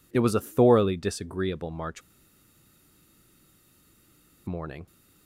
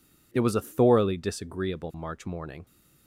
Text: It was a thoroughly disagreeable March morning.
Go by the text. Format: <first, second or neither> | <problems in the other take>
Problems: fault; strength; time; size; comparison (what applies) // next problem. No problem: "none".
second | pauses between "March" and "morning"; strong; at 2.0 s; 2.4 s long